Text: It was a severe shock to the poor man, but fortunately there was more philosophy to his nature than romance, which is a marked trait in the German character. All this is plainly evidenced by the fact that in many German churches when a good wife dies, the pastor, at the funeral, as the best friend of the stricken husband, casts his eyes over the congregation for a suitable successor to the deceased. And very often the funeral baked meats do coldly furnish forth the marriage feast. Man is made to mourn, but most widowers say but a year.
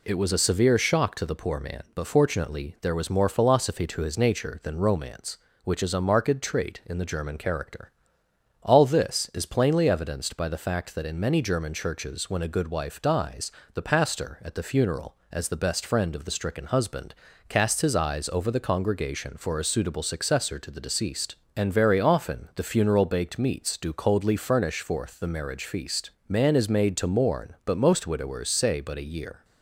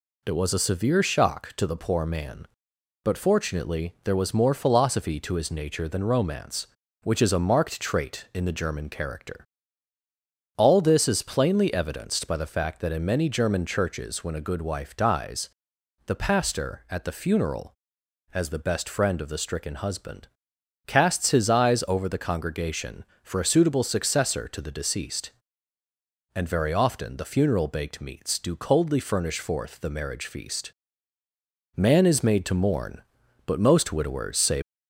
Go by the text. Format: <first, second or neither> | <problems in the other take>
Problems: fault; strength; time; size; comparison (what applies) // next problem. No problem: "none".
first | stops before "but a year"; at 34.6 s